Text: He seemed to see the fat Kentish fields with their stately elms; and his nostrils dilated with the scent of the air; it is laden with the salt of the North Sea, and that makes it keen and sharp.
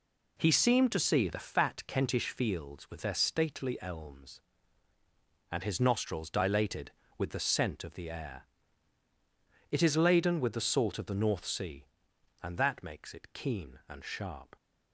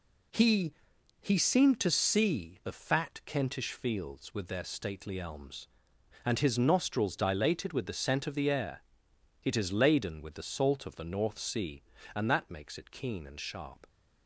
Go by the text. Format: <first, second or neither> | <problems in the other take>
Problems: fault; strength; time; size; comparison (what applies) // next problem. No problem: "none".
first | says "He" twice; at 1.2 s